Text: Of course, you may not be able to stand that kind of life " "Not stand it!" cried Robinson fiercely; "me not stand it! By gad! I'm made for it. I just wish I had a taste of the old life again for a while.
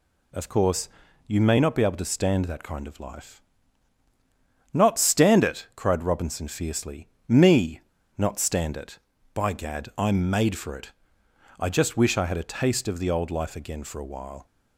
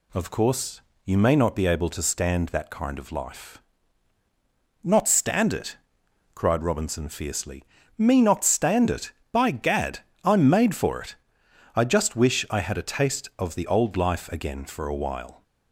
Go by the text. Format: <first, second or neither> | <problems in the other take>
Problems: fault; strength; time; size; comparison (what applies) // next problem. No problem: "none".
second | pauses between "me" and "not"; slight; at 7.8 s; 0.36 s long